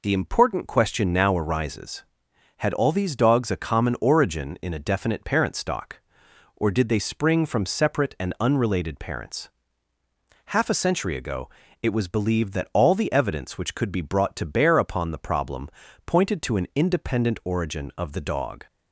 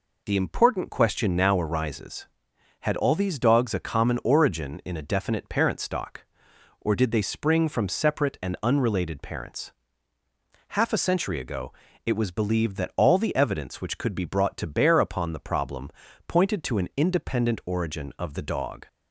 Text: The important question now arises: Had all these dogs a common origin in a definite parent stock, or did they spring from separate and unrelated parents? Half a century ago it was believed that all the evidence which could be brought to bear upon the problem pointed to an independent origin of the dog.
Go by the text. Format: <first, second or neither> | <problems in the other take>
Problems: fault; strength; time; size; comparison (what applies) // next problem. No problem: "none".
neither | pauses between "ago" and "it"; slight; the same in both // pauses between "problem" and "pointed"; slight; the same in both